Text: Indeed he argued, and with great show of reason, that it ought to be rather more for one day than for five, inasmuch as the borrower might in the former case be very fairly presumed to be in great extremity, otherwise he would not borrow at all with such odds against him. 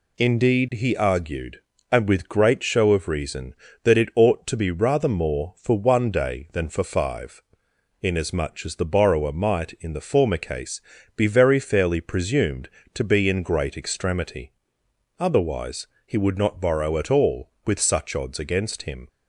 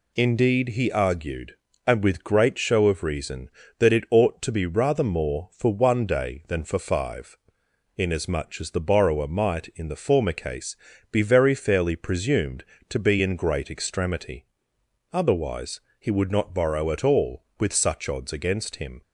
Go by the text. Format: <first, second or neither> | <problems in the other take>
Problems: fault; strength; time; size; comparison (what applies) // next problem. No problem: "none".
neither | pauses between "case" and "be"; slight; the same in both // pauses between "otherwise" and "he"; slight; the same in both